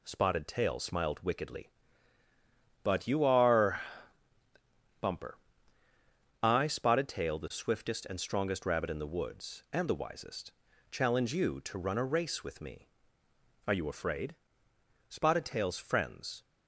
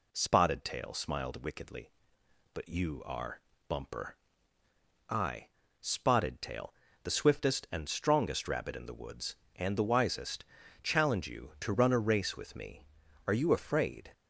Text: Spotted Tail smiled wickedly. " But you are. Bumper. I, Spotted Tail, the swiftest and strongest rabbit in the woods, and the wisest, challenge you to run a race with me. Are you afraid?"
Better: second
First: goes on to say "Spotted Tail's friends"; from 15.0 s on; 1.3 s long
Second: none

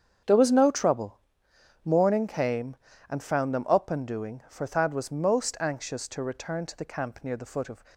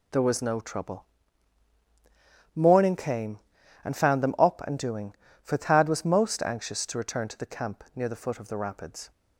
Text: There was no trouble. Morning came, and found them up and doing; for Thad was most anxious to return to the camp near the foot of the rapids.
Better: second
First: starts louder than the rest; strong; until 1.8 s; 7.5 dB // stops before "the rapids"; at 7.9 s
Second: none

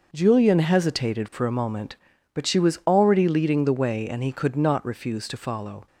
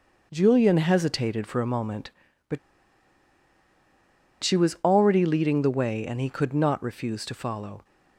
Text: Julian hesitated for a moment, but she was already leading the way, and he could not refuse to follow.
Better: first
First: none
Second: pauses between "but" and "she"; strong; at 2.5 s; 1.8 s long

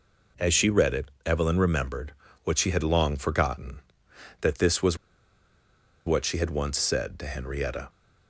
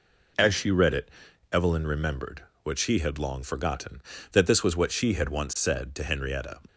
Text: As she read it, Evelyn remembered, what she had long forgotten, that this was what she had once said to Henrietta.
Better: second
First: pauses between "was" and "what"; at 4.9 s; 1.0 s long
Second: none

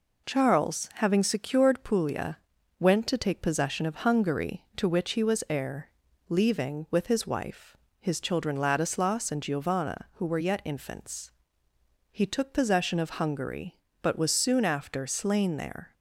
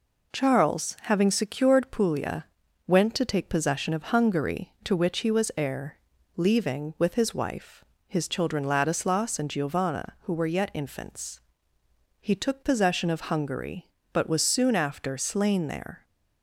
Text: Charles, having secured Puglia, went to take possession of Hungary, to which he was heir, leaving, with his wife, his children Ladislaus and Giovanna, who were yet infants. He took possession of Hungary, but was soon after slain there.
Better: neither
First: none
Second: none

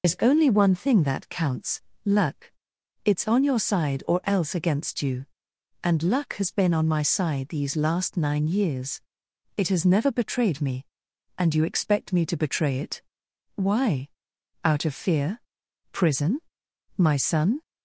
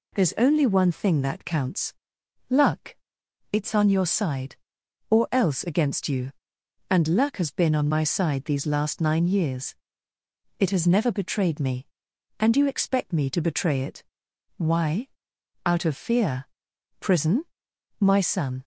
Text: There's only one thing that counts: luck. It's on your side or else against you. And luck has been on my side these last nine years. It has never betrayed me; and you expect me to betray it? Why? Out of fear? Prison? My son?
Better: second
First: loses the start of "There's"; at 0.0 s; 100 ms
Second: none

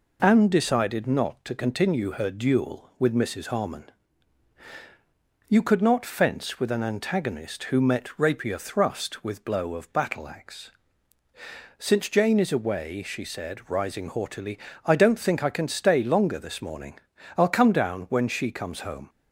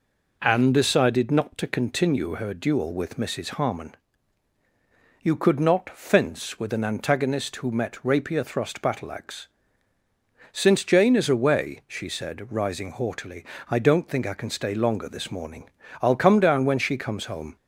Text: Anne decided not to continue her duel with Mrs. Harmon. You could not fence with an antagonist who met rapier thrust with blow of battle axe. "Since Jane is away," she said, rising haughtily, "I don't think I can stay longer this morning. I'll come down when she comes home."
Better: first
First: none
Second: skips "with blow of"; at 8.7 s

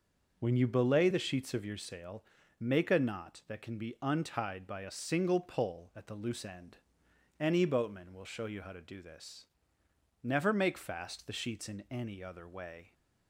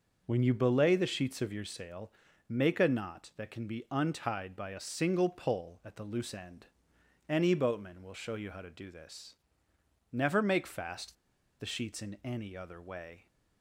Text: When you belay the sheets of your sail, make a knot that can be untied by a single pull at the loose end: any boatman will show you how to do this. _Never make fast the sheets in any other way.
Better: first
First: none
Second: starts louder than the rest; noticeable; until 1.2 s; 6 dB // pauses between "fast" and "the"; noticeable; at 11.1 s; 0.46 s long

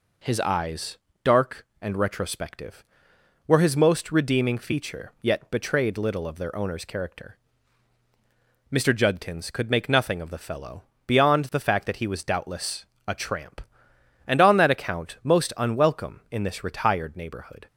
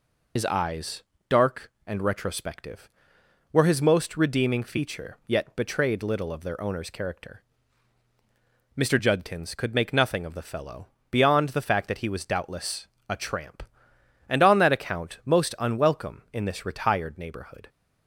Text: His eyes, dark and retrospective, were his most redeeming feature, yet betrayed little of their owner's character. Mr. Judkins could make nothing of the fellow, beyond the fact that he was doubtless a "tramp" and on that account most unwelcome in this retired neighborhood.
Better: first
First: pauses between "doubtless" and "a"; slight; at 12.8 s; 0.20 s long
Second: loses the start of "His"; at 0.3 s; 80 ms // pauses between "doubtless" and "a"; slight; at 12.8 s; 0.20 s long

